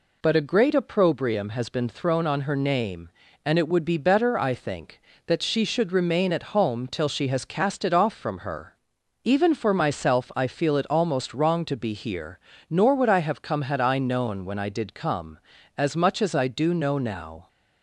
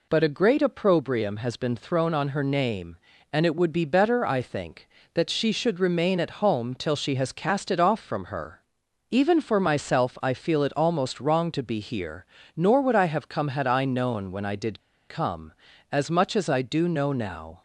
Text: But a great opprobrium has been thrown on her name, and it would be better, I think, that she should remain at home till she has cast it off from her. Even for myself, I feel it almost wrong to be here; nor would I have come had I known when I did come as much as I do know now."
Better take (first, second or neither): first